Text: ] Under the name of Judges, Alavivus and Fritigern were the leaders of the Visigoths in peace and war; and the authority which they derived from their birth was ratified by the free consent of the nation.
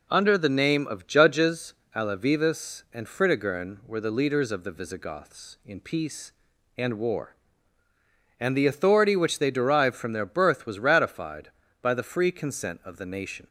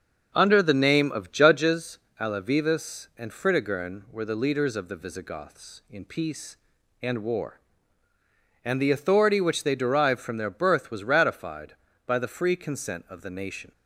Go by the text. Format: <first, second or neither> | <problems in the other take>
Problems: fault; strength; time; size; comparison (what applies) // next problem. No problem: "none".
first | starts louder than the rest; until 1.6 s; 6 dB